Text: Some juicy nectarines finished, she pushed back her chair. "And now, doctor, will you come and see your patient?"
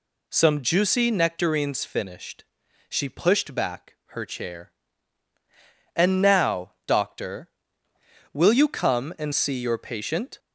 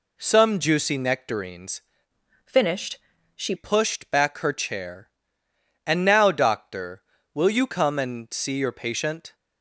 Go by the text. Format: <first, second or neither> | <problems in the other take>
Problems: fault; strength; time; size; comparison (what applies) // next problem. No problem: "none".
first | changes voice from "finished" to "she"; from 2.4 to 3.5 s; 1.1 s long